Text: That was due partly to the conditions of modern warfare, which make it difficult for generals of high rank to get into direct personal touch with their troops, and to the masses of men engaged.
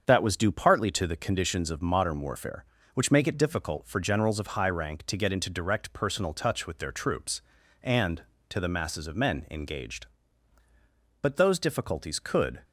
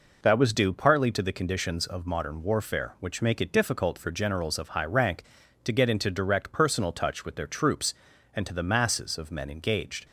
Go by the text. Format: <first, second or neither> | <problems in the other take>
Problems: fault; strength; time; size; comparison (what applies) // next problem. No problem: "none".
second | starts louder than the rest; until 1.0 s; 7 dB // goes on to say "But those difficulties could"; from 11.2 s on; 1.4 s long